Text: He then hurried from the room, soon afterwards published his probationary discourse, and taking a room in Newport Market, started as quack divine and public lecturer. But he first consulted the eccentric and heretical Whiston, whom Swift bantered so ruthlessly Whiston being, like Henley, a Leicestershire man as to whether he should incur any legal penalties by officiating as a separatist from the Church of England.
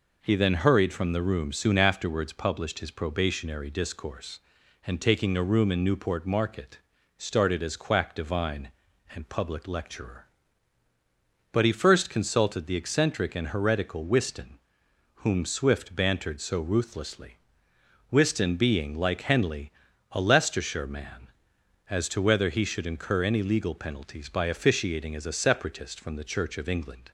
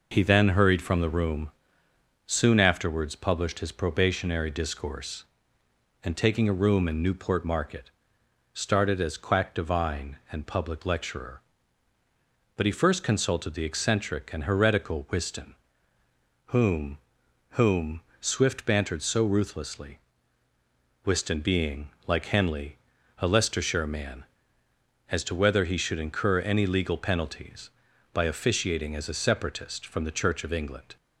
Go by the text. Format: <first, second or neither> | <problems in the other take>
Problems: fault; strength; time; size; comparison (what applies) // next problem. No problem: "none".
first | says "whom" twice; at 17.5 s // pauses between "ruthlessly" and "Whiston"; at 19.9 s; 1.0 s long; noticeable in the first